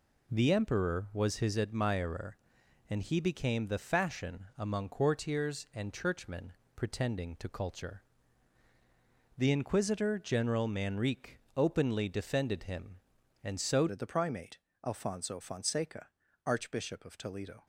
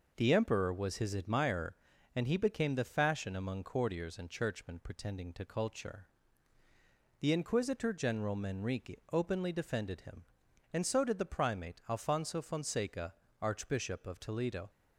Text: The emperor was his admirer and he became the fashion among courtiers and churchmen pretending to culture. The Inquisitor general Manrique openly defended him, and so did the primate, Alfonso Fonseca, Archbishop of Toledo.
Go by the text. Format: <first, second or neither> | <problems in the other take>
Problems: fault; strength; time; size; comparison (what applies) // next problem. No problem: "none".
second | pauses between "churchmen" and "pretending"; slight; at 6.5 s; 0.24 s long // pauses between "Manrique" and "openly"; slight; at 11.3 s; 0.18 s long // changes voice at "did"; from 13.8 s on; 3.8 s long